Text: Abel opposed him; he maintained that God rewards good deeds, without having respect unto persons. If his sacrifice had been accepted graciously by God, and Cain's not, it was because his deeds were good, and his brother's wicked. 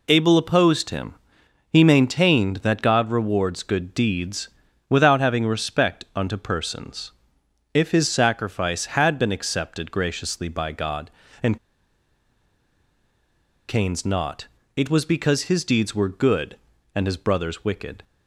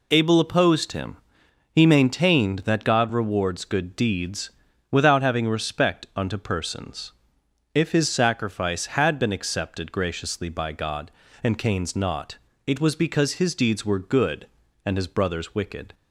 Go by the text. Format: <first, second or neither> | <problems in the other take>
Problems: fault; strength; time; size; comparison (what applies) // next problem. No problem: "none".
second | pauses between "and" and "Cain's"; strong; at 11.5 s; 2.1 s long